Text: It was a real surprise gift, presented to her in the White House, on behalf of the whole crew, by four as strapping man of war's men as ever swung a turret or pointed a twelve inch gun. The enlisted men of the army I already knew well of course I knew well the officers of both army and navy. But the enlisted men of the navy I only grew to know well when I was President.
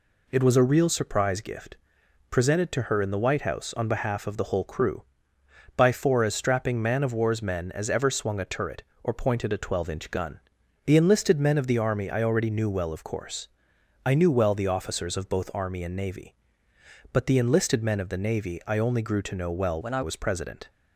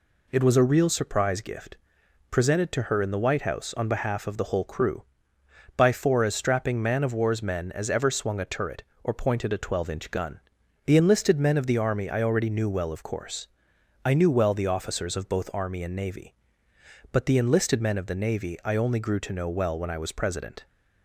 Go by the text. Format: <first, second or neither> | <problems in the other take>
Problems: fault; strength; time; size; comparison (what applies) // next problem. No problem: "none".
second | pauses between "course" and "I"; noticeable; at 13.4 s; 0.56 s long; noticeable in the second // changes voice from "when" to "I"; from 19.8 to 20.0 s; 0.2 s long